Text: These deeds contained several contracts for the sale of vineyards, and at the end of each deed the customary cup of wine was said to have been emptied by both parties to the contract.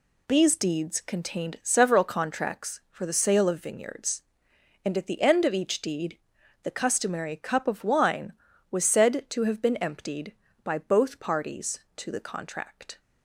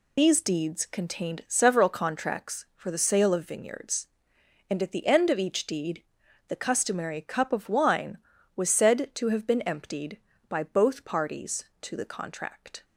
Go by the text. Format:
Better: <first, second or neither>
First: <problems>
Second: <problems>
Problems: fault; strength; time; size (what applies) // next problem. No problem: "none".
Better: first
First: pauses between "deed" and "the"; noticeable; at 6.1 s; 0.46 s long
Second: loses the start of "These"; at 0.1 s; 55 ms // pauses between "deed" and "the"; noticeable; at 6.0 s; 0.46 s long